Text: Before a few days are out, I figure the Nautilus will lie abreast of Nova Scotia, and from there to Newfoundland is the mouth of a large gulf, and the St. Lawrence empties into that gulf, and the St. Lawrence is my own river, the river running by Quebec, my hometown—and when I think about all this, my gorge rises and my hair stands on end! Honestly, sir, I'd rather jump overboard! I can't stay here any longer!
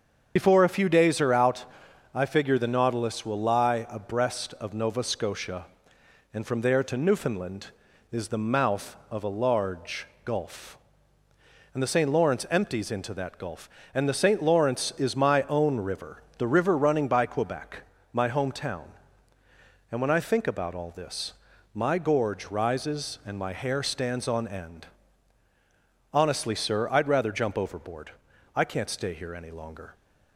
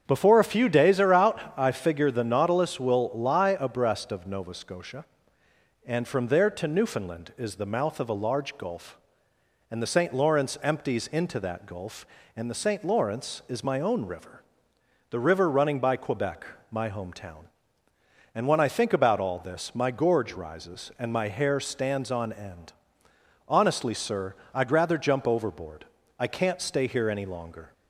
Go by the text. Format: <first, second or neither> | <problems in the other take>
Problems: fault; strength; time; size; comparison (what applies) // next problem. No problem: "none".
second | loses the start of "Before"; at 0.3 s; 55 ms // starts louder than the rest; until 1.3 s; 7 dB; strong in the second // pauses between "large" and "gulf"; slight; at 10.0 s; 0.20 s long